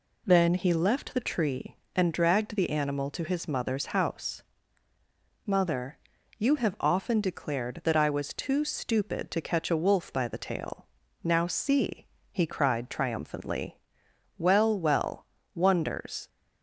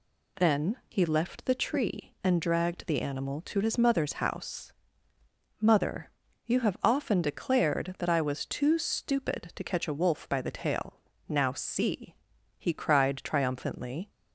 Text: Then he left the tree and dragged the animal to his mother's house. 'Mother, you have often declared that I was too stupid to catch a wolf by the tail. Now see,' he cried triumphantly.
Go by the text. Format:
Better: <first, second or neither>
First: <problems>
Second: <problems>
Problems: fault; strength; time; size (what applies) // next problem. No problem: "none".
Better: second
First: goes on to say "Well well wonders"; strong; from 14.3 s on; 1.9 s long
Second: none